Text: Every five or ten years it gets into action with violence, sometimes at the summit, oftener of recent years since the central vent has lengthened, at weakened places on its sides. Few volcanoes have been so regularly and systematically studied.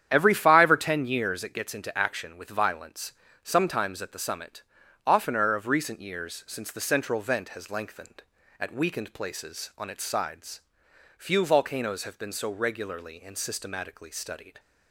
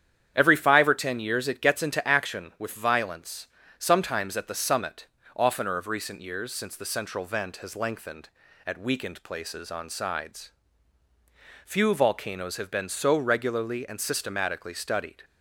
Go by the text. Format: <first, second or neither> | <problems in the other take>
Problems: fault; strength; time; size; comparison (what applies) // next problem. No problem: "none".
first | starts louder than the rest; strong; until 1.3 s; 9.5 dB; strong in the first // skips "its"; at 9.9 s